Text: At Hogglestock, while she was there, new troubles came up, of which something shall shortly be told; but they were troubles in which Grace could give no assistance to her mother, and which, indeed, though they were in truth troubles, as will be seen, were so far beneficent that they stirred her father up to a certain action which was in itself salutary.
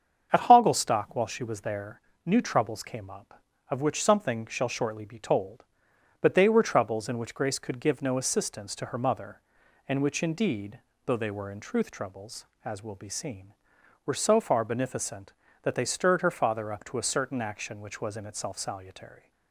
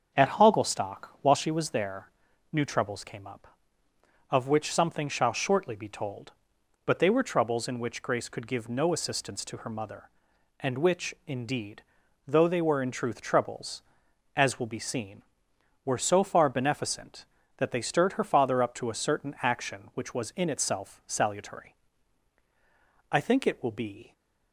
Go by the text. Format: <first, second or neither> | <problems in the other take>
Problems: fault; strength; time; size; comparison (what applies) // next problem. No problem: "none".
first | starts louder than the rest; strong; until 1.3 s; 8 dB; strong in the first // goes on to say "I think it will be"; noticeable; from 23.1 s on; 1.0 s long